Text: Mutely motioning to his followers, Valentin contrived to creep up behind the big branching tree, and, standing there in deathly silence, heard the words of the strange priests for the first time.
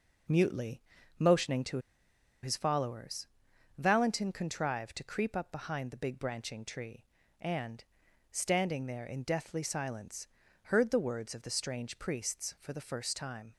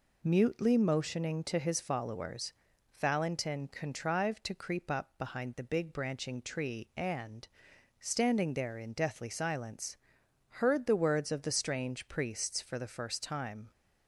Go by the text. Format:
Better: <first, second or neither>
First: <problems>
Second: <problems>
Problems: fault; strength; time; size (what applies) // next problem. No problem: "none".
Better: second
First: pauses between "Mutely" and "motioning"; at 0.8 s; 0.38 s long // pauses between "to" and "his"; noticeable; at 1.7 s; 0.64 s long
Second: none